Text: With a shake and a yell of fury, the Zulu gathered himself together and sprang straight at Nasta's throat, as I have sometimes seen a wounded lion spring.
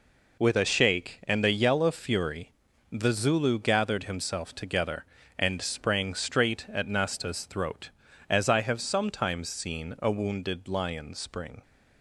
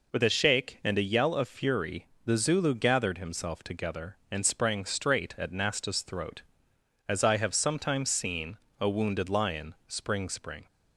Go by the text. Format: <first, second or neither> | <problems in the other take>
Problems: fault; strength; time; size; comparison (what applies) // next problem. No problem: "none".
first | pauses between "seen" and "a"; slight; at 8.5 s; 0.24 s long // says "spring" twice; at 10.2 s